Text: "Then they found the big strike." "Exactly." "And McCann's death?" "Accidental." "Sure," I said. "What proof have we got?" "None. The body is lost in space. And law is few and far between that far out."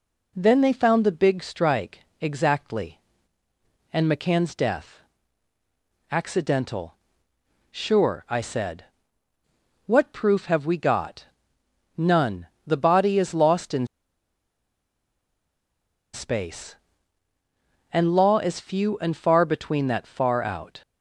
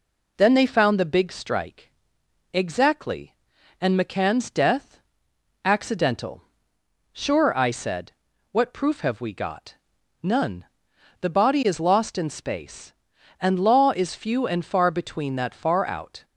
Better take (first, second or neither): second